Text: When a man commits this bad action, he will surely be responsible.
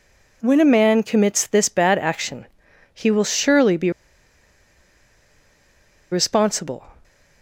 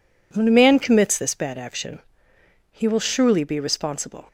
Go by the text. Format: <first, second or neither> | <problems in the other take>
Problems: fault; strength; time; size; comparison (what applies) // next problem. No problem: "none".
second | pauses between "be" and "responsible"; strong; at 3.9 s; 2.2 s long